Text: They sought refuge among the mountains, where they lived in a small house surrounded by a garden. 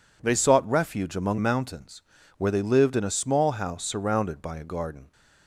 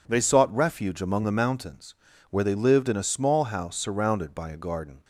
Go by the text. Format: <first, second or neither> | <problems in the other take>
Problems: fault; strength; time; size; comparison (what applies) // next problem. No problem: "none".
second | skips "the"; at 1.3 s